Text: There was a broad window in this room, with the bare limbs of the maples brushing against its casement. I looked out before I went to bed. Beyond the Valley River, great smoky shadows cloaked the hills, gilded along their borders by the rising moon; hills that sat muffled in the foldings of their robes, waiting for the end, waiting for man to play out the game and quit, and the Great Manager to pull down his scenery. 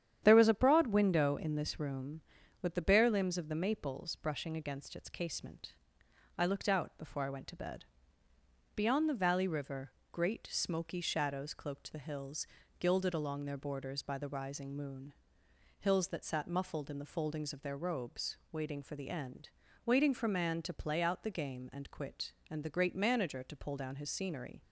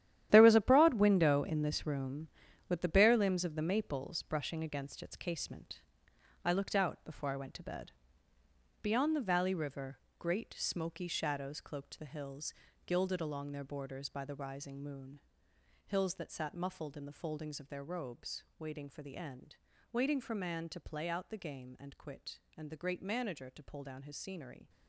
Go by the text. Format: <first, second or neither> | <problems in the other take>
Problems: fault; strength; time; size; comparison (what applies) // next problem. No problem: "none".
first | gets quieter; strong; throughout; 11.5 dB // starts louder than the rest; strong; until 1.3 s; 11.5 dB; strong in the first